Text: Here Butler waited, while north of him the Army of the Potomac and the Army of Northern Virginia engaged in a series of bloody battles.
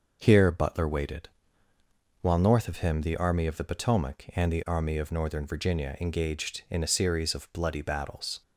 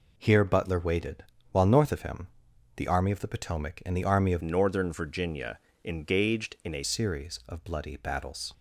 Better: first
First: none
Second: pauses between "him" and "the"; noticeable; at 2.2 s; 0.48 s long // changes voice from "Northern" to "a"; from 4.4 to 6.8 s; 2.4 s long // pauses between "Virginia" and "engaged"; slight; at 5.5 s; 0.24 s long

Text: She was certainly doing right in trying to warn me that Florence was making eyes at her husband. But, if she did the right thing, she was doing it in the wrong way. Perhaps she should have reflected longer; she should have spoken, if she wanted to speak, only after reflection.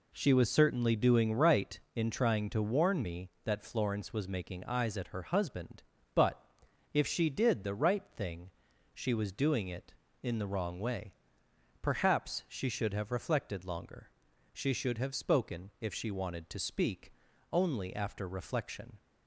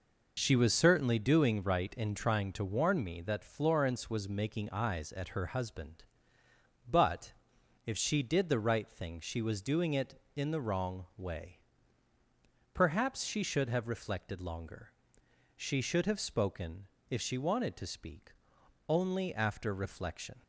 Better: neither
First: none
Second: none

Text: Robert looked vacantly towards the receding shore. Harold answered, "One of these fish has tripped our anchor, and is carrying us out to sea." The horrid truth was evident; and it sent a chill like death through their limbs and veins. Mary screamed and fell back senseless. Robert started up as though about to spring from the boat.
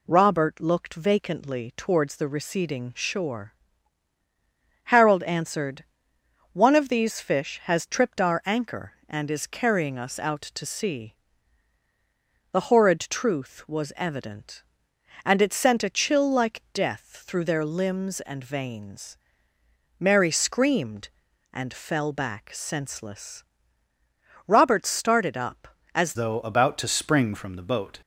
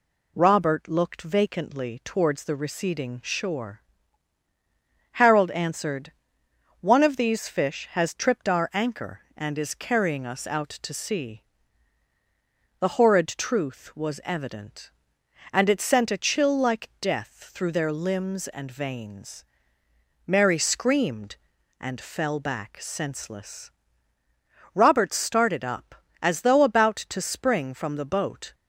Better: second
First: changes voice at "though"; from 26.1 s on; 1.8 s long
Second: none

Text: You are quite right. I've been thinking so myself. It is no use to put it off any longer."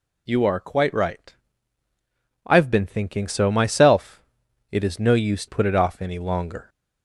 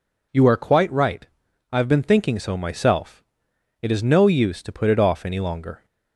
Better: second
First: skips "to"; at 5.4 s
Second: none

